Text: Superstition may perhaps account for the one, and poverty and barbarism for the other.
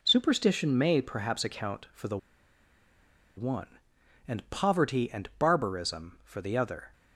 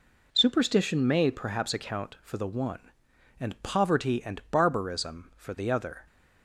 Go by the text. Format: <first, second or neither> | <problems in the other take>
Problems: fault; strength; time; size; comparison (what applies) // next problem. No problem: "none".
second | pauses between "the" and "one"; at 2.1 s; 1.2 s long